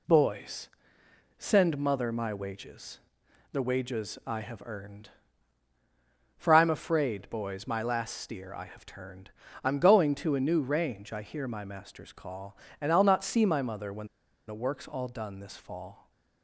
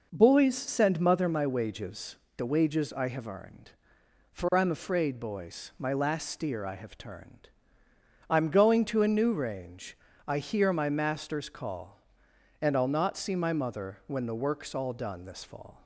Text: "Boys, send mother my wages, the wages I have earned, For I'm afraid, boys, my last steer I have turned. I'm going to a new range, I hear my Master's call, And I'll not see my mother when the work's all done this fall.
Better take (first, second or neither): second